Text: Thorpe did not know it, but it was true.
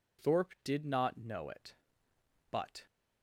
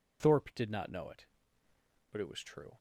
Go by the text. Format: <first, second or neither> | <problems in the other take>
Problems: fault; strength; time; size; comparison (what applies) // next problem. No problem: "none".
second | stops before "it was true"; at 2.8 s